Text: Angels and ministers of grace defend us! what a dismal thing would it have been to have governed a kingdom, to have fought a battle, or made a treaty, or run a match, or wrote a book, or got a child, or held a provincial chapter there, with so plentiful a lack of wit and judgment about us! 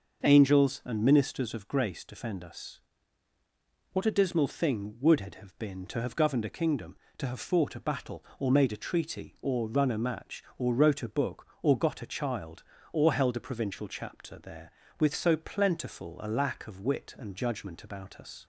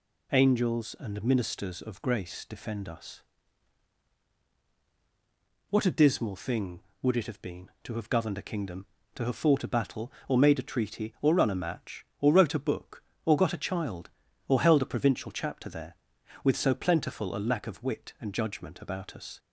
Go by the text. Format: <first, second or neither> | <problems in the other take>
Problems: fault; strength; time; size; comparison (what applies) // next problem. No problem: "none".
neither | none